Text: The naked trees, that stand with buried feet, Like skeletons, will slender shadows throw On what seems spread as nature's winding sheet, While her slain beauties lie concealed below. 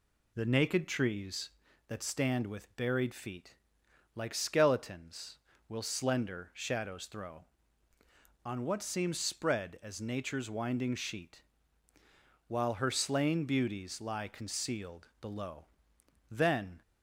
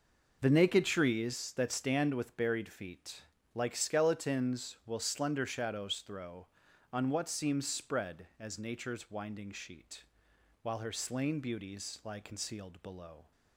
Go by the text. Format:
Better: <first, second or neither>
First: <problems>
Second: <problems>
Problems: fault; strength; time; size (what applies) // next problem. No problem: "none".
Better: second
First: goes on to say "Then"; from 16.3 s on; 0.50 s long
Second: none